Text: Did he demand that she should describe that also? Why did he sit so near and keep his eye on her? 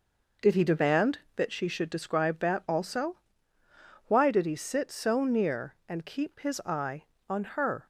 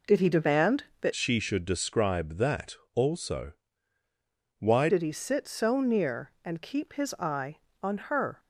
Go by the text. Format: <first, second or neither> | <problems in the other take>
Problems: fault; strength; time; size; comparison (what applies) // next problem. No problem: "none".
first | changes voice from "she" to "Why"; from 1.1 to 4.8 s; 3.7 s long // pauses between "that" and "also"; slight; at 2.7 s; 0.18 s long